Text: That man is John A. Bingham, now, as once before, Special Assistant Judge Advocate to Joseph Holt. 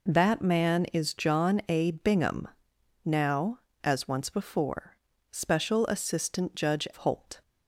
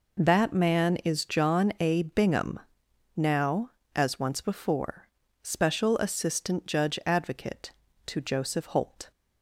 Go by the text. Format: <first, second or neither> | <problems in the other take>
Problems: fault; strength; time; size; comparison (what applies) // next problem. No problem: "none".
second | skips "Advocate to Joseph"; at 6.9 s